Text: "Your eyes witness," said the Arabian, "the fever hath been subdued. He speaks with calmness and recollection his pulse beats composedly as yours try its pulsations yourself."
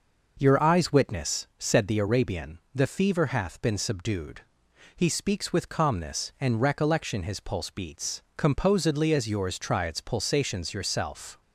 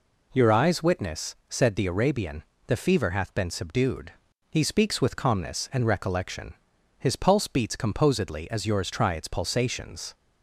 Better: first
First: none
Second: pauses between "recollection" and "his"; at 6.5 s; 0.44 s long // stops before "yourself"; at 10.1 s

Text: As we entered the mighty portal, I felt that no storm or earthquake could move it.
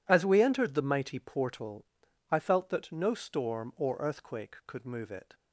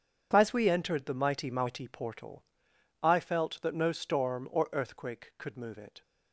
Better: first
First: none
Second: says "mighty" twice; at 1.4 s

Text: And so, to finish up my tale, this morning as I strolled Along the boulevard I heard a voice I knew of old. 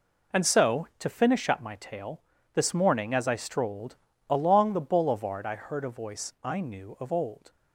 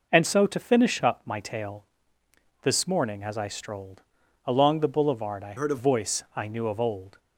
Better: first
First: pauses between "strolled" and "Along"; slight; at 3.9 s; 0.32 s long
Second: pauses between "strolled" and "Along"; at 4.0 s; 0.42 s long // changes voice from "heard" to "a"; from 5.5 to 5.7 s; 0.2 s long

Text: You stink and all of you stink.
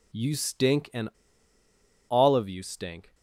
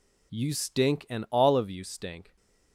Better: second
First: pauses between "and" and "all"; at 1.0 s; 1.0 s long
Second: none

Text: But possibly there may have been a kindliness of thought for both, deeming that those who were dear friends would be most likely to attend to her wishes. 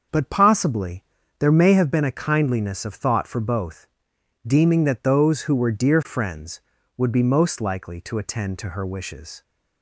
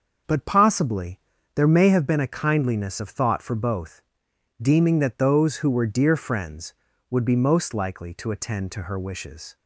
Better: neither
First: starts louder than the rest; until 1.4 s; 6 dB // pauses between "possibly" and "there"; slight; at 1.0 s; 0.34 s long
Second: starts louder than the rest; until 1.6 s; 6 dB // pauses between "possibly" and "there"; slight; at 1.2 s; 0.34 s long

